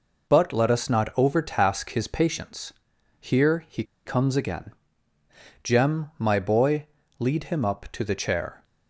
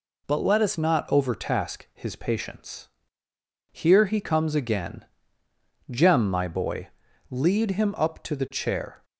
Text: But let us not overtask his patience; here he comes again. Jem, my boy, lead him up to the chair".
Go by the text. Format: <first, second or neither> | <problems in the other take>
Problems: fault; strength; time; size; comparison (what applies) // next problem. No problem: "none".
second | pauses between "he" and "comes"; slight; at 3.8 s; 0.22 s long